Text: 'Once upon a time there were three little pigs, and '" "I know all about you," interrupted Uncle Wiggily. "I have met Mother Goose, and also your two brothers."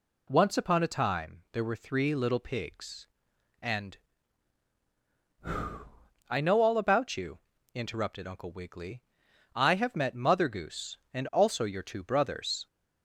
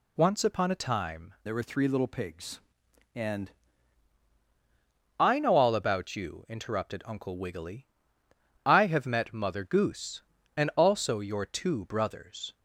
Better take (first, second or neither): first